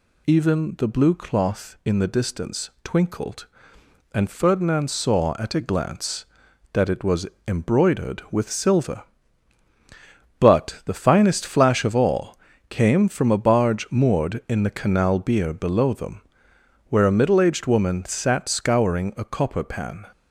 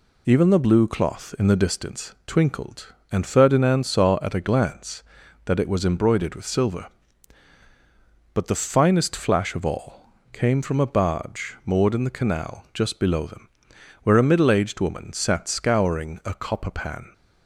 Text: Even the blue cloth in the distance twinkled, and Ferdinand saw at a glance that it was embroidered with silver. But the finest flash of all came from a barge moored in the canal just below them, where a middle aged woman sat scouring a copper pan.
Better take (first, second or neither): second